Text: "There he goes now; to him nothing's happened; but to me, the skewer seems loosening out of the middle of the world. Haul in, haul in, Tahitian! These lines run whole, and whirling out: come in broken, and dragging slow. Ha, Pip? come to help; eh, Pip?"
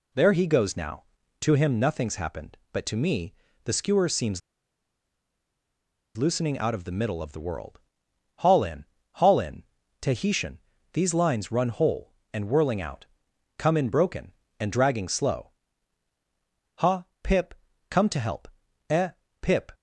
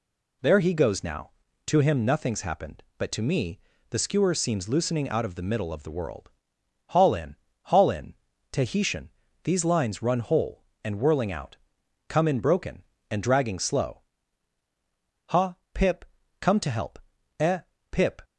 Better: second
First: pauses between "seems" and "loosening"; strong; at 4.4 s; 1.7 s long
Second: none

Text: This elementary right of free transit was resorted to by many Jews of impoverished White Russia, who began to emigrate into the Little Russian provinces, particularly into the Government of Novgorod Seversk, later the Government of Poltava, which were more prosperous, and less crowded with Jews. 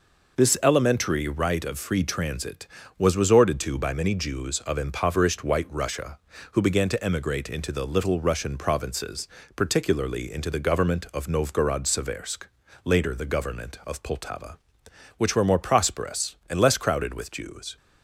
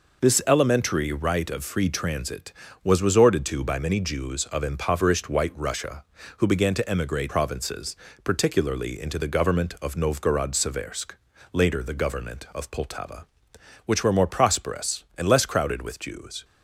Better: first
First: none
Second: skips "into the Little Russian"; at 7.2 s

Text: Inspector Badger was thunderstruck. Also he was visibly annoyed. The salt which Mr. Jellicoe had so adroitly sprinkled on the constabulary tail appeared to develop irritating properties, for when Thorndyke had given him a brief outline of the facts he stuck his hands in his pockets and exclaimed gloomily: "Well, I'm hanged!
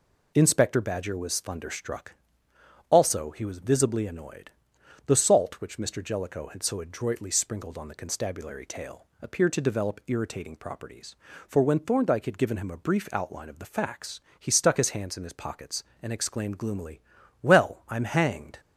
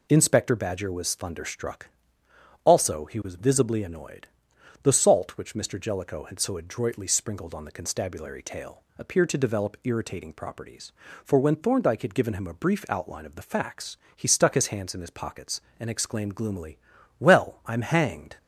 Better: neither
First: pauses between "tail" and "appeared"; slight; at 9.0 s; 0.16 s long // pauses between "facts" and "he"; slight; at 14.2 s; 0.18 s long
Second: pauses between "tail" and "appeared"; slight; at 8.8 s; 0.16 s long // pauses between "facts" and "he"; slight; at 13.9 s; 0.18 s long

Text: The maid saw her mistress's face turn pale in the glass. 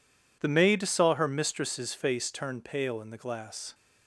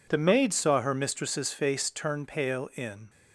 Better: first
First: none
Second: stops before "the glass"; at 3.0 s

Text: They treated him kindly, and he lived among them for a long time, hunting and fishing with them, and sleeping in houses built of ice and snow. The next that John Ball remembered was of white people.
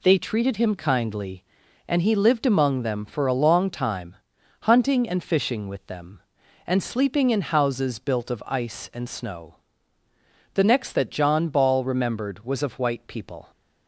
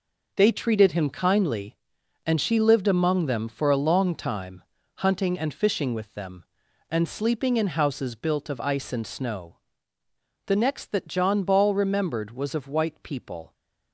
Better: first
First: none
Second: says "she" for "he"; at 2.4 s

